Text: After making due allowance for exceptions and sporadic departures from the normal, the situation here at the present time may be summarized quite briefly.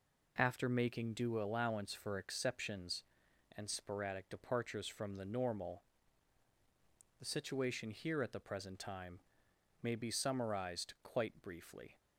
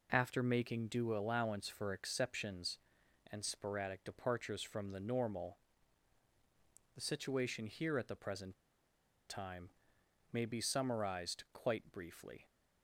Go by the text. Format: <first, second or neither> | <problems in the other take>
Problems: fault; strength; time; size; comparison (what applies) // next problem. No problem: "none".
first | pauses between "present" and "time"; noticeable; at 8.5 s; 0.75 s long // pauses between "time" and "may"; noticeable; at 9.6 s; 0.62 s long; noticeable in the first